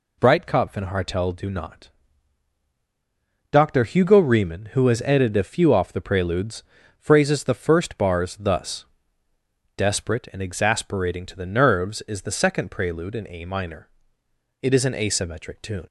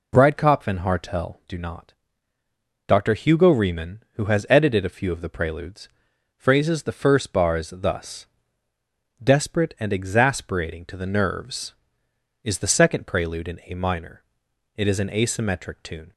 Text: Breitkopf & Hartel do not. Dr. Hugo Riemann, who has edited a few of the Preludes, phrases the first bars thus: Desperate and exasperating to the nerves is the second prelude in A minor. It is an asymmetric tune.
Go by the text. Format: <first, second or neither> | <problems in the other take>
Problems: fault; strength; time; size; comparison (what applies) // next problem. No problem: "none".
second | says "off" for "of"; at 5.7 s